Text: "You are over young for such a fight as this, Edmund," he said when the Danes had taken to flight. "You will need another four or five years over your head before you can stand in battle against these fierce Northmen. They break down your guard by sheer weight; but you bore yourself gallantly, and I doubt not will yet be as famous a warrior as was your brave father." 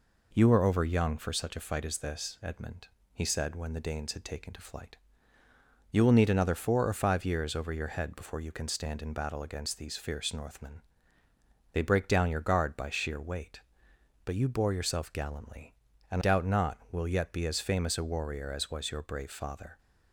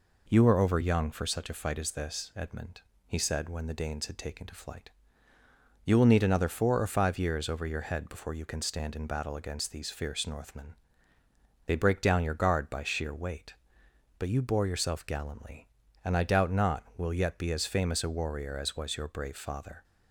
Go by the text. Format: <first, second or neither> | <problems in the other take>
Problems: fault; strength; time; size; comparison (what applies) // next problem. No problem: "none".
second | skips "I"; at 16.2 s